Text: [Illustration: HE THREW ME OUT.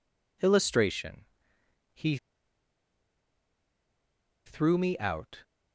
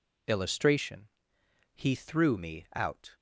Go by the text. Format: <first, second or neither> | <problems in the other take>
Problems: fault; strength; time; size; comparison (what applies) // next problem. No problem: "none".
second | pauses between "HE" and "THREW"; strong; at 2.1 s; 2.2 s long